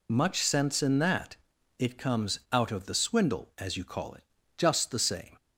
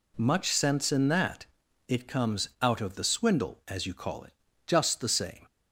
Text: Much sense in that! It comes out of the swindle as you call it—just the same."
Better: second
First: loses the start of "Much"; at 0.0 s; 50 ms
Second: none

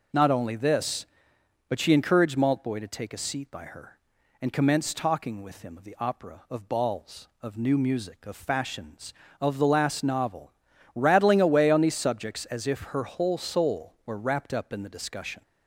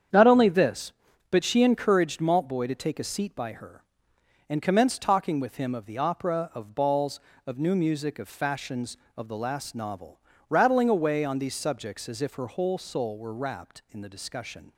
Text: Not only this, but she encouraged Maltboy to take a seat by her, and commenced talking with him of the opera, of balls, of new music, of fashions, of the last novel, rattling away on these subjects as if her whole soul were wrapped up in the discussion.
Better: first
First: none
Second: starts louder than the rest; strong; until 1.5 s; 8 dB // skips "up"; at 13.8 s

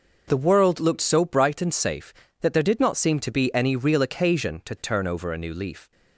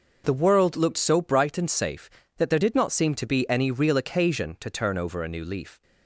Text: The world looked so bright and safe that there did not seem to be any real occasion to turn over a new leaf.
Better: neither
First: none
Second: none

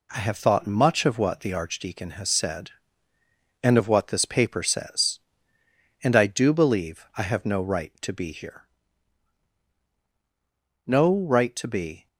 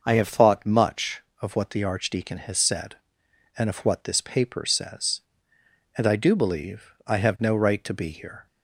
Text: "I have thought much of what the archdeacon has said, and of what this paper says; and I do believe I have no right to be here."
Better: second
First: goes on to say "No right to be"; noticeable; from 10.8 s on; 1.2 s long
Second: none

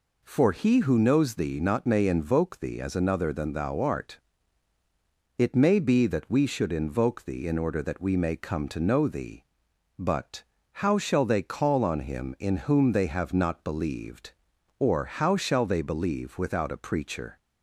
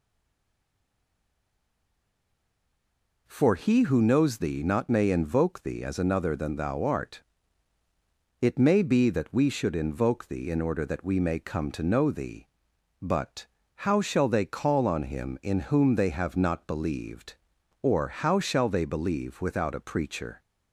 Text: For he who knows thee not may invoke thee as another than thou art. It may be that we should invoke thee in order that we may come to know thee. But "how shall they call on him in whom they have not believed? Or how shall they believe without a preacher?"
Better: first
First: pauses between "But" and "how"; slight; at 10.4 s; 0.28 s long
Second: stays silent before the first word; strong; until 3.2 s; 3.2 s long // pauses between "But" and "how"; slight; at 13.4 s; 0.28 s long

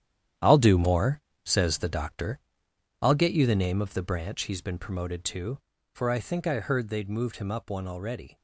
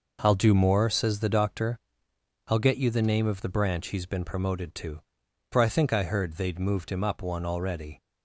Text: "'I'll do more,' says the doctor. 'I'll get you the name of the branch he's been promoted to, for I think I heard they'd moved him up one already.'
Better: second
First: gets quieter; strong; throughout; 9.5 dB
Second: none

